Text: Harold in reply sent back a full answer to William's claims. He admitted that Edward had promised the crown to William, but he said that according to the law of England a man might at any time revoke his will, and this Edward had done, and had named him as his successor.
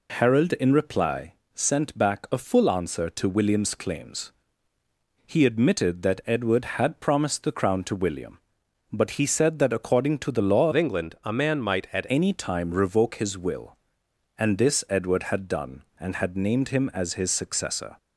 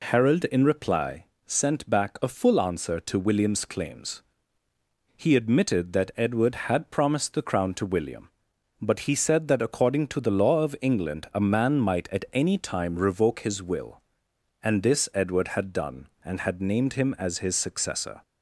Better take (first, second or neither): second